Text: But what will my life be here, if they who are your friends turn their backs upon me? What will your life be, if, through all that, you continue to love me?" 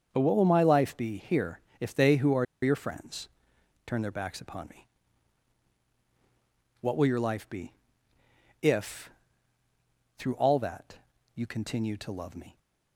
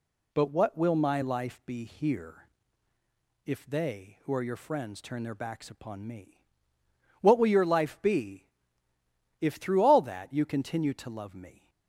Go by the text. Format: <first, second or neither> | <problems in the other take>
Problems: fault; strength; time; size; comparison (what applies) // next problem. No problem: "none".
second | starts louder than the rest; until 1.1 s; 6.5 dB // pauses between "are" and "your"; slight; at 2.4 s; 0.17 s long // pauses between "friends" and "turn"; noticeable; at 3.2 s; 0.58 s long